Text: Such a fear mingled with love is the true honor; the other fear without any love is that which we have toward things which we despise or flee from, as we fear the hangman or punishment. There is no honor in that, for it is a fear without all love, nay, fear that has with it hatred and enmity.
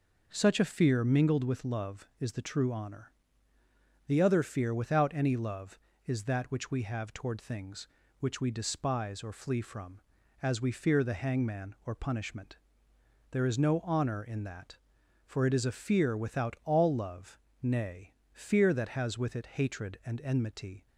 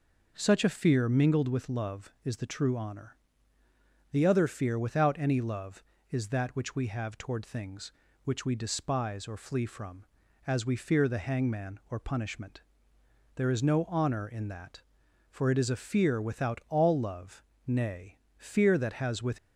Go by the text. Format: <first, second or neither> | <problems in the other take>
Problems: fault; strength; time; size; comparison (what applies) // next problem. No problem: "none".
first | stops before "it hatred and enmity"; at 19.3 s